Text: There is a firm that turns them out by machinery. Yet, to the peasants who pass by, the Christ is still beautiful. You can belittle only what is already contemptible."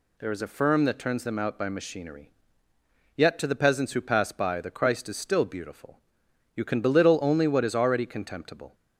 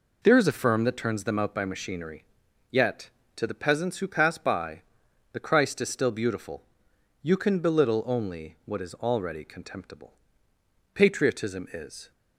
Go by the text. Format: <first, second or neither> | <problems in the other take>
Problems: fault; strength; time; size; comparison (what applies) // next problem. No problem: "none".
first | goes on to say "Patriotism is"; noticeable; from 10.9 s on; 1.1 s long